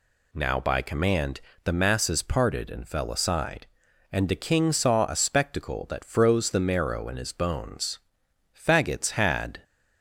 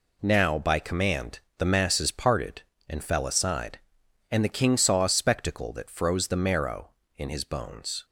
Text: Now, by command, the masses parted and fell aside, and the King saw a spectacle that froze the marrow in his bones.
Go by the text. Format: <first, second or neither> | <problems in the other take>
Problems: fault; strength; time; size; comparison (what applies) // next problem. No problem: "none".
second | goes on to say "Faggots had"; noticeable; from 8.5 s on; 1.0 s long